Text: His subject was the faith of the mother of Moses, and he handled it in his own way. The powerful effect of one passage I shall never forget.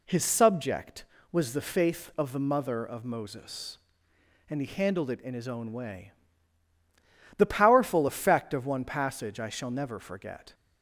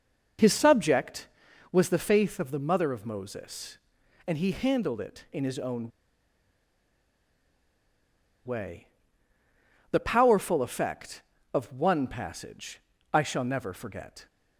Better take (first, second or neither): first